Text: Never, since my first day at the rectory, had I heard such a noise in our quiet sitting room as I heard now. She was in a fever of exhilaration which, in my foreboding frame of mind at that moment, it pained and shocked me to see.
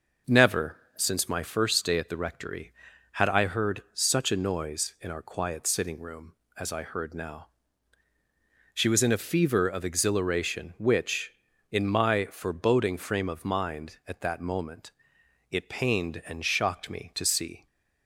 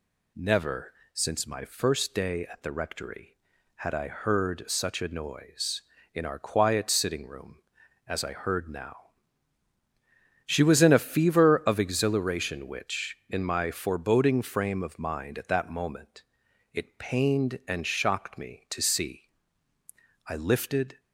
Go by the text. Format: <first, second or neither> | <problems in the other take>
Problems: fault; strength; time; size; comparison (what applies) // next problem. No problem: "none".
first | goes on to say "I lifted"; noticeable; from 20.2 s on; 0.72 s long